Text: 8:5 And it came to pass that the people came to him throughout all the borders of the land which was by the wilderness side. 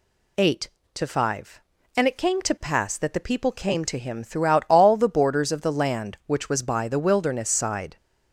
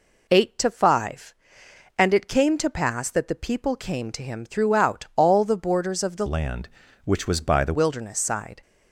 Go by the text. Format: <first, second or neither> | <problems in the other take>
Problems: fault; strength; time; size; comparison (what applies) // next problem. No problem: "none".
first | changes voice from "land" to "the"; from 6.2 to 7.7 s; 1.5 s long